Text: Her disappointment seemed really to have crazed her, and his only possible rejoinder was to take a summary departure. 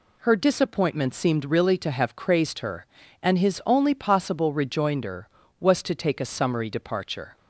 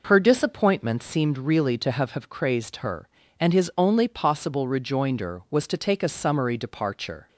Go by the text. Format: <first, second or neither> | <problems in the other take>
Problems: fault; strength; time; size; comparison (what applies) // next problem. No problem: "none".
first | says "have" twice; at 2.1 s